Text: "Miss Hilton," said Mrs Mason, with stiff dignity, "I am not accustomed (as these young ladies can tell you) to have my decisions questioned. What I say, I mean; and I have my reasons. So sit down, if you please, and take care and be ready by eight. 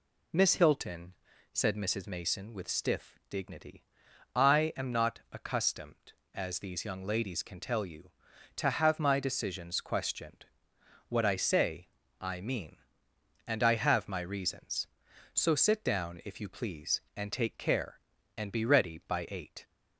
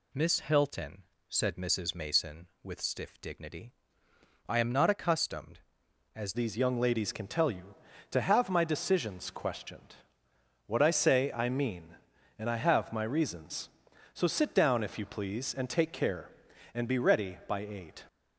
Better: first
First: none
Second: changes voice at "these"; from 6.3 s on; 11.7 s long

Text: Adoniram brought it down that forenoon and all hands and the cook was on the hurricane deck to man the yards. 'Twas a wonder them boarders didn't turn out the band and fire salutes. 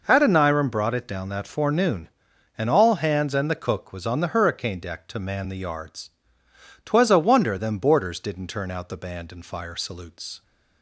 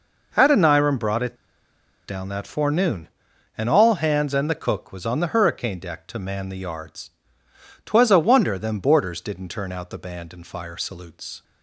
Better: first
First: none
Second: pauses between "it" and "down"; noticeable; at 1.3 s; 0.72 s long

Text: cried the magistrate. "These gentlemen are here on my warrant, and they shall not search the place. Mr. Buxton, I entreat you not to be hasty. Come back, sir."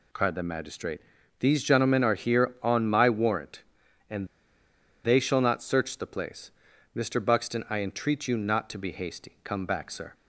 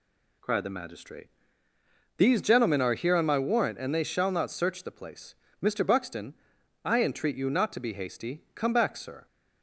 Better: second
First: pauses between "and" and "they"; noticeable; at 4.2 s; 0.77 s long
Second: none

